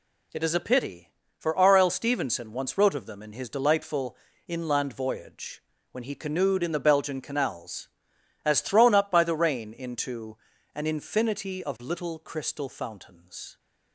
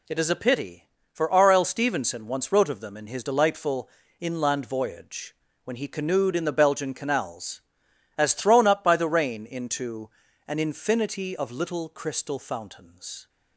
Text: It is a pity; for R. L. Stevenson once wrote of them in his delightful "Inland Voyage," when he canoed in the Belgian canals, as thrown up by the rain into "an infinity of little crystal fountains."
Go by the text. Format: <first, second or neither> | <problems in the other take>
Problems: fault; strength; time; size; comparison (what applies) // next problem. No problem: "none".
neither | pauses between "delightful" and "Inland"; slight; the same in both // pauses between "into" and "an"; slight; the same in both